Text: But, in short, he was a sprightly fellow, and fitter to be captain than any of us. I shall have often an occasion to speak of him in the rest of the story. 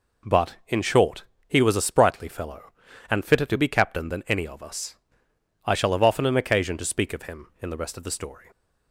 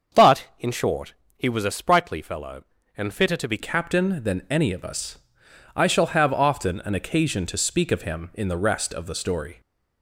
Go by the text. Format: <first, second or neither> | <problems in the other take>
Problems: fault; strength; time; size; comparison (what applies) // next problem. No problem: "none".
first | starts louder than the rest; until 1.5 s; 7 dB // changes voice at "captain"; from 3.5 s on; 6.0 s long